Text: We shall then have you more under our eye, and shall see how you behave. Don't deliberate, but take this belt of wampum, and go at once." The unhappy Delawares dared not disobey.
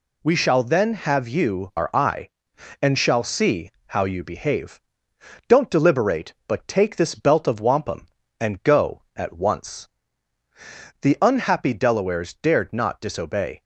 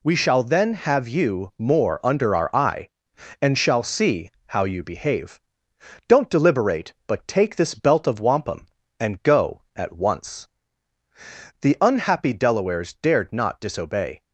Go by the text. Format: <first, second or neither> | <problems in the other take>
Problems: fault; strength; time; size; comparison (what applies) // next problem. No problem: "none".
second | skips "more under"; at 1.7 s // pauses between "see" and "how"; slight; at 3.6 s; 0.18 s long; slight in the second